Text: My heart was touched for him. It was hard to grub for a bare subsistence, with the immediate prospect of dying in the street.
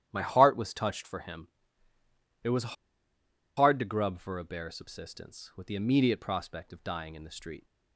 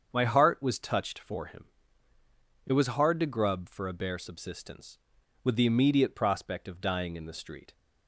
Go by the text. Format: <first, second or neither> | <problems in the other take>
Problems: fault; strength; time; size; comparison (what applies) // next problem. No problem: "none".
second | starts louder than the rest; strong; until 1.1 s; 11 dB; strong in the second // pauses between "was" and "hard"; noticeable; at 2.7 s; 0.82 s long